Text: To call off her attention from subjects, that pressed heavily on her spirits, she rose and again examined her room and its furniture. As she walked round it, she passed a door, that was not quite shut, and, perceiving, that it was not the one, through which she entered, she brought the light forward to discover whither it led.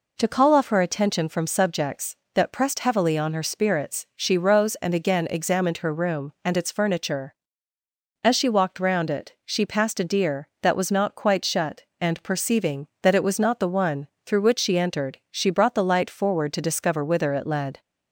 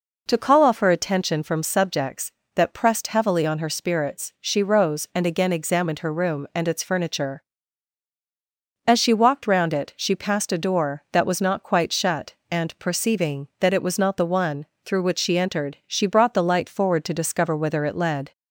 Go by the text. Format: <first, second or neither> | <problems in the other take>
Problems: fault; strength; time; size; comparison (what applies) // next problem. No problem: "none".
second | says "deer" for "door"; at 10.0 s